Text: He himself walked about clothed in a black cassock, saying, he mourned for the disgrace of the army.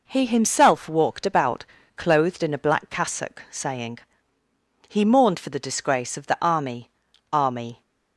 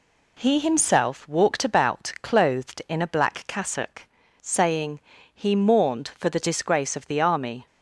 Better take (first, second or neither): second